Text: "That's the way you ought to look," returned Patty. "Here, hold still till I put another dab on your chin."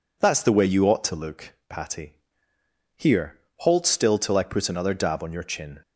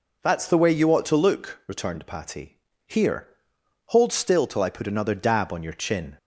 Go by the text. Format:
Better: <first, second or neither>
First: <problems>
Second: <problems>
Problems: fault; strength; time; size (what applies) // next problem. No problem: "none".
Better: second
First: skips "returned"; at 1.6 s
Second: none